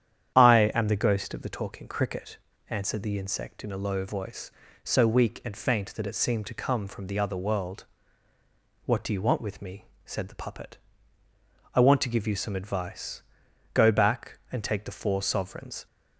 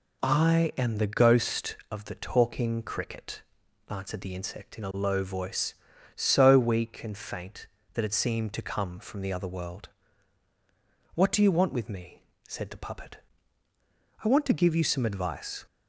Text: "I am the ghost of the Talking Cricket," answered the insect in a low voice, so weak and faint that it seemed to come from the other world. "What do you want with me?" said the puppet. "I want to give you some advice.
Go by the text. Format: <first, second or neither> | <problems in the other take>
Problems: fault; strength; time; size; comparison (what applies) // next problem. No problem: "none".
second | starts louder than the rest; strong; until 1.3 s; 9.5 dB // goes on to say "Go back and take the four sovereigns"; strong; from 13.7 s on; 2.1 s long